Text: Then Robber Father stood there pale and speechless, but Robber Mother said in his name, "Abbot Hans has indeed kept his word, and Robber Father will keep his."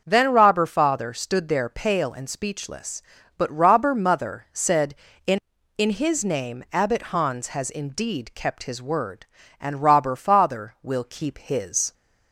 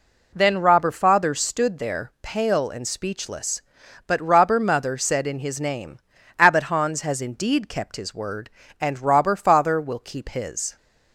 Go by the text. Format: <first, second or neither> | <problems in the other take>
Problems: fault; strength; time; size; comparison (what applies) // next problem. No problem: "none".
second | starts louder than the rest; until 1.0 s; 6.5 dB // says "in" twice; at 5.7 s